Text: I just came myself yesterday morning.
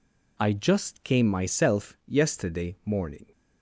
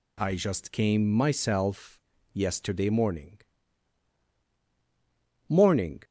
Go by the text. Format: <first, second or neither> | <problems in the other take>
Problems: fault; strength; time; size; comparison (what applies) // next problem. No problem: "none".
first | pauses between "myself" and "yesterday"; slight; at 2.0 s; 0.32 s long // says "morning" twice; at 5.4 s